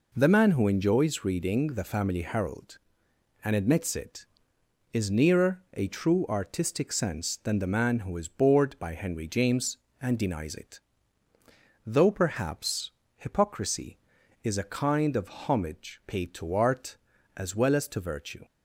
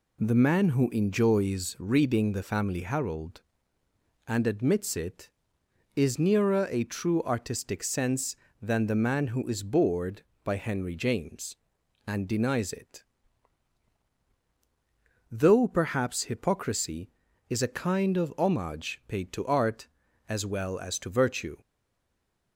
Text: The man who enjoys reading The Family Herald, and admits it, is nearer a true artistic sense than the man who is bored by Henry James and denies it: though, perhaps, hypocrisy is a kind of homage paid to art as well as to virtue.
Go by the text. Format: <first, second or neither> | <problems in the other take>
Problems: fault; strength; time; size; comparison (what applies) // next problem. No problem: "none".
first | stays silent after the last word; slight; from 21.6 s on; 0.9 s long